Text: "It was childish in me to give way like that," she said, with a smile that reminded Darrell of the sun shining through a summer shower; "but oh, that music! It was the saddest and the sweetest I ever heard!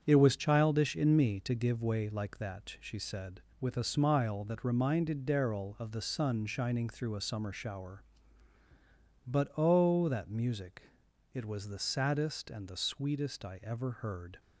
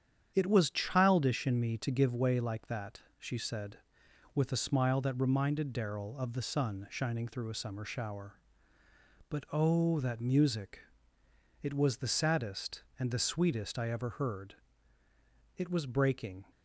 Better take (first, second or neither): first